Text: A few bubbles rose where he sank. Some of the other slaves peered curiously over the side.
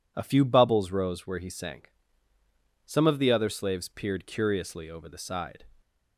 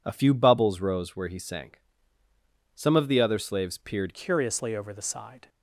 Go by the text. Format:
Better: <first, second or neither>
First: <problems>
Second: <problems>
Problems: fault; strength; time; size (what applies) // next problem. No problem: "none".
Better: first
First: none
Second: changes voice at "curiously"; from 4.1 s on; 1.3 s long